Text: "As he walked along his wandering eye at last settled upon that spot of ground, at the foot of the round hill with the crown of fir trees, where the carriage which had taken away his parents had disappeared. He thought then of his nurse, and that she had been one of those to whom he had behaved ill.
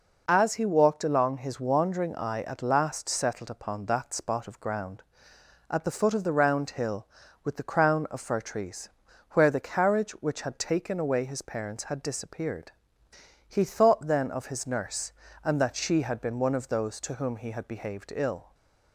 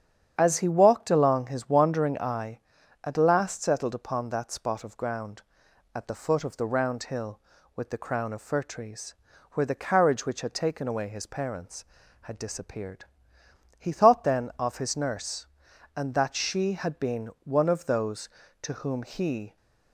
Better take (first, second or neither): first